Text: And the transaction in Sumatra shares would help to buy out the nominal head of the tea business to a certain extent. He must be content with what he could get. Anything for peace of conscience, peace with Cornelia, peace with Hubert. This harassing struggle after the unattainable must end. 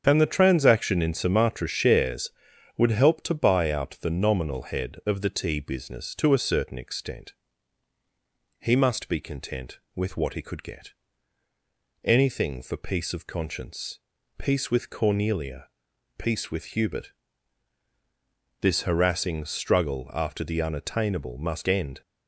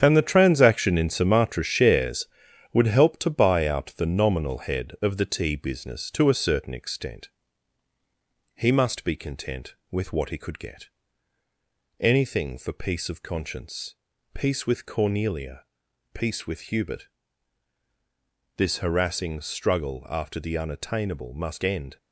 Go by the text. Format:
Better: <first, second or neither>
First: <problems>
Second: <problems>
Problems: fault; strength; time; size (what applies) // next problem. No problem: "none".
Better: first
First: starts louder than the rest; strong; until 1.0 s; 8 dB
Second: gets quieter; strong; throughout; 8 dB // starts louder than the rest; strong; until 1.0 s; 8.5 dB